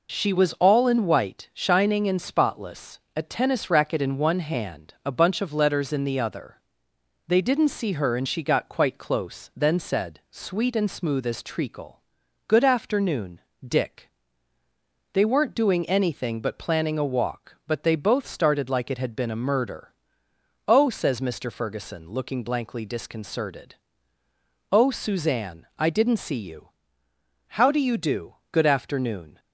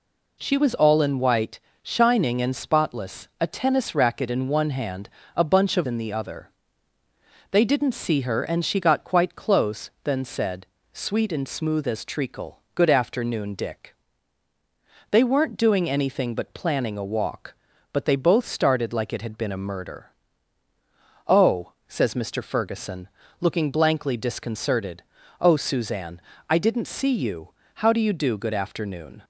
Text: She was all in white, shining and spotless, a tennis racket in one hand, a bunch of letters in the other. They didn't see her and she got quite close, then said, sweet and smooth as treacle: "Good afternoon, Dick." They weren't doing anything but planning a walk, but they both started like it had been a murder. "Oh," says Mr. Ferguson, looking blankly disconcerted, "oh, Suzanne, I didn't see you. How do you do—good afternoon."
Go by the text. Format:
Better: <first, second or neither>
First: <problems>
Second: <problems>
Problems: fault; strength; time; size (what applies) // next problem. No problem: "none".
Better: first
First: none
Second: skips "letters"; at 5.8 s